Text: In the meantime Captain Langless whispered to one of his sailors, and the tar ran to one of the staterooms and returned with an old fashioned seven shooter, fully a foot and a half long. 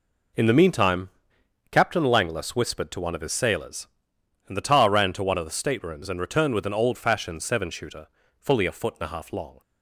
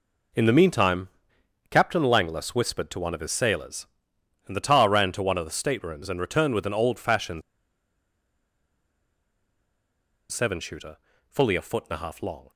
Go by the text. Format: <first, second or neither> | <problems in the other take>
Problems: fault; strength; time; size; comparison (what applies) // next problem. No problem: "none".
first | pauses between "meantime" and "Captain"; noticeable; at 1.0 s; 0.60 s long; noticeable in the first // pauses between "fashioned" and "seven"; strong; at 7.4 s; 2.9 s long